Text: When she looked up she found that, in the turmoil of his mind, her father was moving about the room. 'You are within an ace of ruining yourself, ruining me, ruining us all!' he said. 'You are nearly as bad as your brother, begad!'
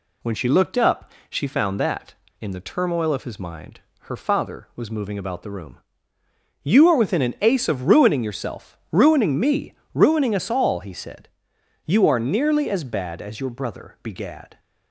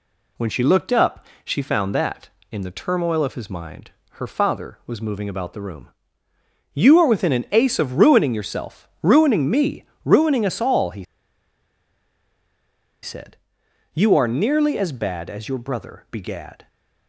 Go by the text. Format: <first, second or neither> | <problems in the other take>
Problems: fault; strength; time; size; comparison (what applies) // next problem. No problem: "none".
first | pauses between "up" and "she"; slight; at 1.2 s; 0.18 s long; slight in the first // pauses between "he" and "said"; strong; at 11.0 s; 1.9 s long